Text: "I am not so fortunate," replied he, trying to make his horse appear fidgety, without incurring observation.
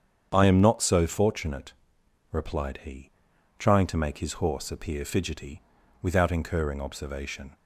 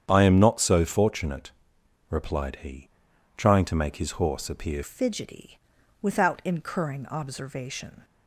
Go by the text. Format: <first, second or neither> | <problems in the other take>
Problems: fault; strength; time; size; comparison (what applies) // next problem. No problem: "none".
first | starts louder than the rest; strong; until 1.1 s; 8.5 dB; strong in the first // changes voice at "fidgety"; from 4.8 s on; 3.2 s long